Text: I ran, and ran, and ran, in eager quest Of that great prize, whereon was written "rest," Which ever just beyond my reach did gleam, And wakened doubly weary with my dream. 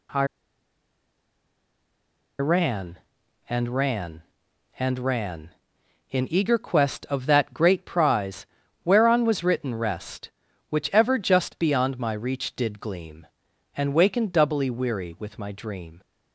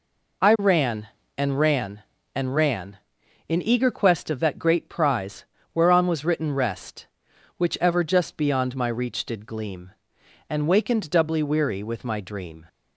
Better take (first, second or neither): second